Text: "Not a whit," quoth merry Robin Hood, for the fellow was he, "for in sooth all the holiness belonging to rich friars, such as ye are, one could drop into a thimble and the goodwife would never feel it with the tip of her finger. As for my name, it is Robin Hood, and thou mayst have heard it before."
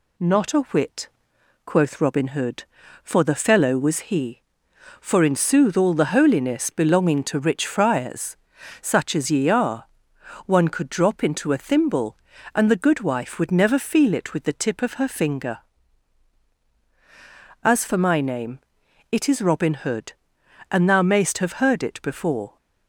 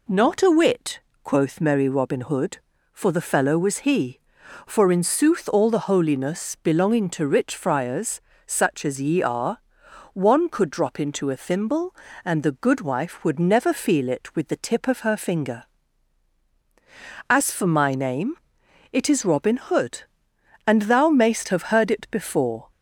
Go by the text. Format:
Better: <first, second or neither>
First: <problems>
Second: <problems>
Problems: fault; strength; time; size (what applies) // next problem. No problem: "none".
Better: second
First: skips "merry"; at 2.0 s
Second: none